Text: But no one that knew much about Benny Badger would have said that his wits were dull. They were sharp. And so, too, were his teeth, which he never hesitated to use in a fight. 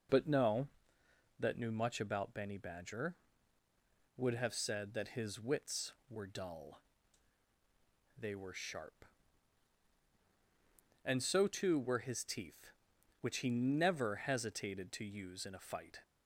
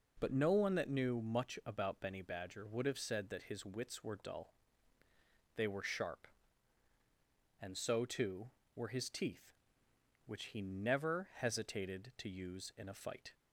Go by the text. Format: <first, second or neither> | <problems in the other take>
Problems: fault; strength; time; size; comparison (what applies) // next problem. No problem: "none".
second | skips "one"; at 1.0 s